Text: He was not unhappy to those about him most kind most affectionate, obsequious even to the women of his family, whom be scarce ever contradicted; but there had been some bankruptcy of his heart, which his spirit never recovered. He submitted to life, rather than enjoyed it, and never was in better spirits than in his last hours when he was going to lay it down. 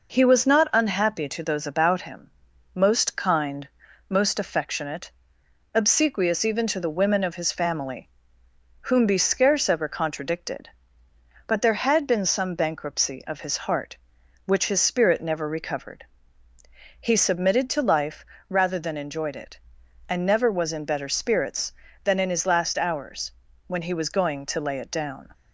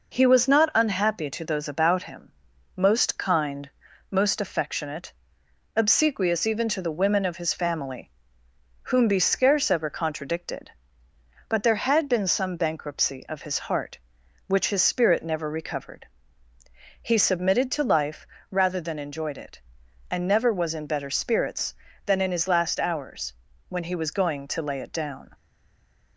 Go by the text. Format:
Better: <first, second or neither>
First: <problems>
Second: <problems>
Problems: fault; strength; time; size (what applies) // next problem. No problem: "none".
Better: first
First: pauses between "him" and "most"; at 2.3 s; 0.44 s long // pauses between "kind" and "most"; at 3.6 s; 0.44 s long // pauses between "hours" and "when"; at 23.3 s; 0.38 s long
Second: pauses between "him" and "most"; at 2.3 s; 0.44 s long // pauses between "kind" and "most"; at 3.6 s; 0.44 s long // pauses between "hours" and "when"; at 23.3 s; 0.38 s long // stays silent after the last word; slight; from 25.3 s on; 0.8 s long